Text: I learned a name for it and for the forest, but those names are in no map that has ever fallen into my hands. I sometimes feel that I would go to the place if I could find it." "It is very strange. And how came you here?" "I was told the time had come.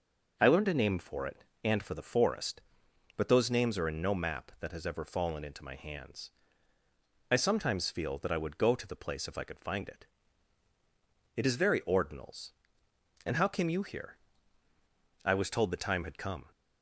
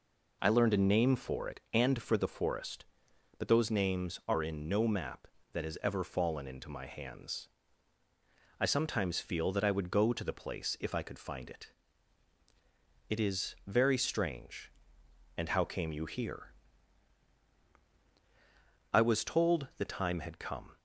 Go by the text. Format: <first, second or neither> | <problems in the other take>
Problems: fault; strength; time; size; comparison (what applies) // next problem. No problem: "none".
second | says "ordinals" for "strange"; at 11.8 s